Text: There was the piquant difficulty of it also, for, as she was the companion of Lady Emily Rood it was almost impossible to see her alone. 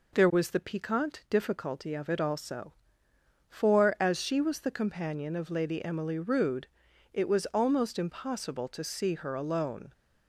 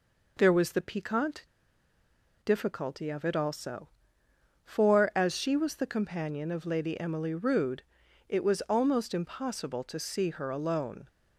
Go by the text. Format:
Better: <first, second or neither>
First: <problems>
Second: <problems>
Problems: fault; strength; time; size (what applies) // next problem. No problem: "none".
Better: first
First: pauses between "Rood" and "it"; at 6.6 s; 0.44 s long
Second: pauses between "piquant" and "difficulty"; noticeable; at 1.4 s; 0.97 s long // pauses between "Rood" and "it"; at 7.8 s; 0.44 s long